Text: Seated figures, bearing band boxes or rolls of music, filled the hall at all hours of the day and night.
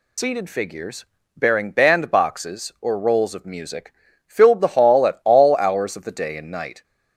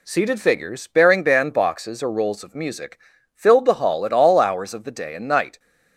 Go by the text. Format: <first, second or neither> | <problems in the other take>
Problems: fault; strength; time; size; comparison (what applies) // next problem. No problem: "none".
second | loses the start of "Seated"; at 0.1 s; 105 ms